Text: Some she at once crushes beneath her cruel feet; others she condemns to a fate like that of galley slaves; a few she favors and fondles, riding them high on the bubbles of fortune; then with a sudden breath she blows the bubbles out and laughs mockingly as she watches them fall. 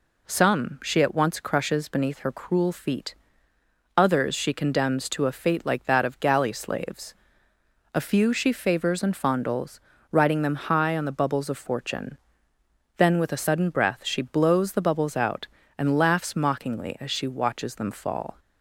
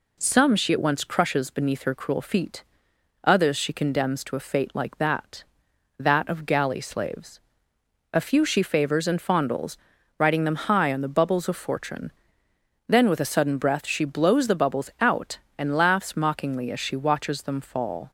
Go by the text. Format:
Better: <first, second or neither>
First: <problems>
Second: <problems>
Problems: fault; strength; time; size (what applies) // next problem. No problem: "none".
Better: first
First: none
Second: says "that" twice; at 5.9 s